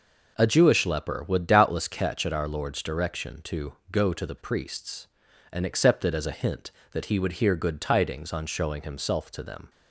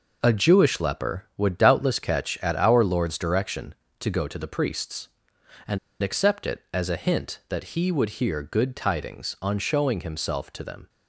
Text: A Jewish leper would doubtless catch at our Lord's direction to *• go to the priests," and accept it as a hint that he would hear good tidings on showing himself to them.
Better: first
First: none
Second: pauses between "and" and "accept"; slight; at 5.7 s; 0.24 s long

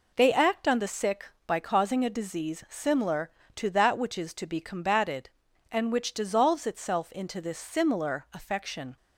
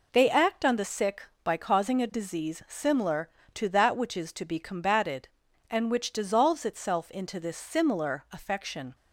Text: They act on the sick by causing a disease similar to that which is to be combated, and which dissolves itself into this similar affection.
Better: neither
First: none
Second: none

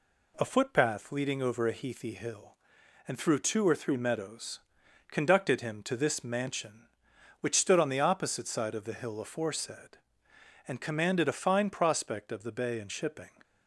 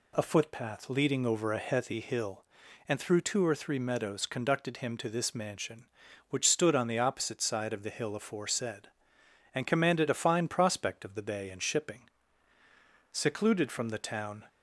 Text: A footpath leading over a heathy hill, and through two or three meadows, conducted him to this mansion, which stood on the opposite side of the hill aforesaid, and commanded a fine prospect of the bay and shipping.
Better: first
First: none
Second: goes on to say "Secluded from the town"; from 13.0 s on; 1.3 s long

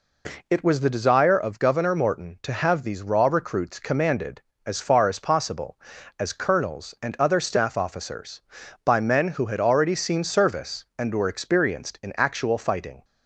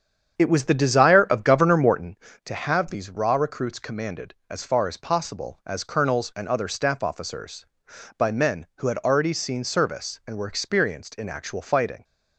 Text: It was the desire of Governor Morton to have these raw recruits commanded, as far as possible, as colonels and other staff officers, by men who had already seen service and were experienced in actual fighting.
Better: first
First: none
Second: starts louder than the rest; strong; until 2.2 s; 8 dB

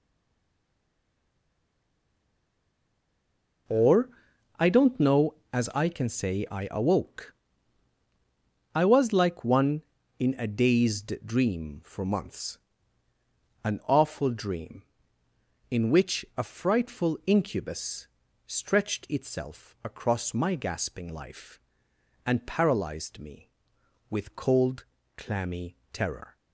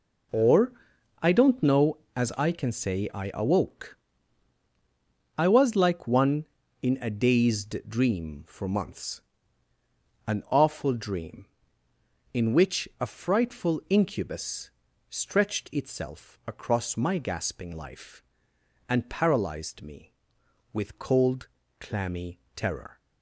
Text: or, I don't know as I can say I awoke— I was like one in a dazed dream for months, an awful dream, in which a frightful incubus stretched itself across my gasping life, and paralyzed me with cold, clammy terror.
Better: second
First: stays silent before the first word; strong; until 3.6 s; 3.6 s long // pauses between "incubus" and "stretched"; at 18.0 s; 0.40 s long // pauses between "clammy" and "terror"; slight; at 25.7 s; 0.16 s long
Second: pauses between "incubus" and "stretched"; at 14.6 s; 0.40 s long // pauses between "clammy" and "terror"; slight; at 22.3 s; 0.16 s long

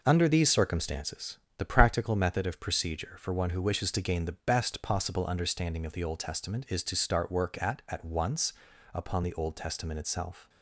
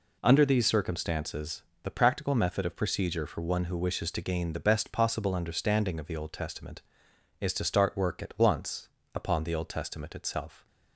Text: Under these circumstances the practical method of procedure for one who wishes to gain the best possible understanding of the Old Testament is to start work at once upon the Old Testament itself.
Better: second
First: pauses between "circumstances" and "the"; slight; at 1.3 s; 0.20 s long // says "at" twice; at 7.8 s // pauses between "once" and "upon"; at 8.5 s; 0.44 s long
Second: pauses between "circumstances" and "the"; slight; at 1.6 s; 0.22 s long // pauses between "once" and "upon"; slight; at 8.8 s; 0.26 s long

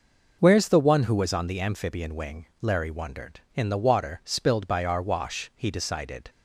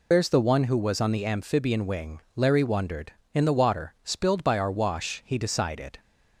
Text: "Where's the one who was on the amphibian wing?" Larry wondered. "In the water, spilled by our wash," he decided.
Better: first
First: none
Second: loses the start of "Where's"; at 0.1 s; 100 ms

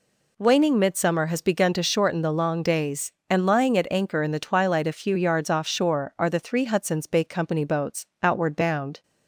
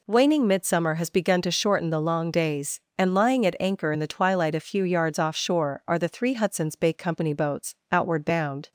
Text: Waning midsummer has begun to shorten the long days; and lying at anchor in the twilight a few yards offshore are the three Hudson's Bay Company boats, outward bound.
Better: neither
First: none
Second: none

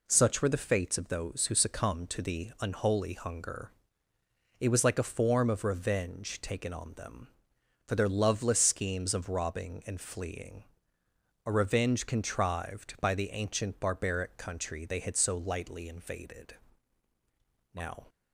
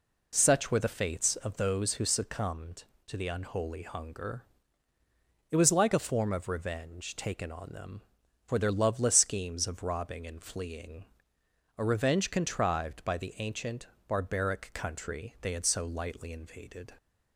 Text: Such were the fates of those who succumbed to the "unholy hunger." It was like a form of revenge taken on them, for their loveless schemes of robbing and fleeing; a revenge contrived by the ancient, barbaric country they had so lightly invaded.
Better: second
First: goes on to say "Now"; slight; from 17.7 s on; 0.32 s long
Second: none

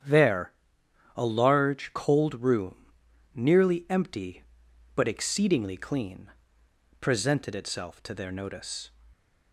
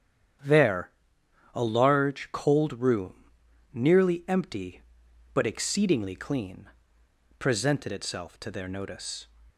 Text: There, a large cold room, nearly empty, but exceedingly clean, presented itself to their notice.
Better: neither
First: starts louder than the rest; strong; until 1.6 s; 9 dB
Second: starts louder than the rest; strong; until 2.0 s; 9 dB

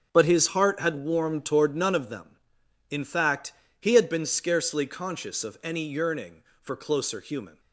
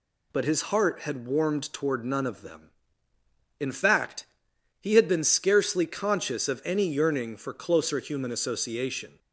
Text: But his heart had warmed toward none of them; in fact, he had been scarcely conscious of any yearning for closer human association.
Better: second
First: starts louder than the rest; noticeable; until 1.1 s; 6 dB // stops before "association"; at 7.5 s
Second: none

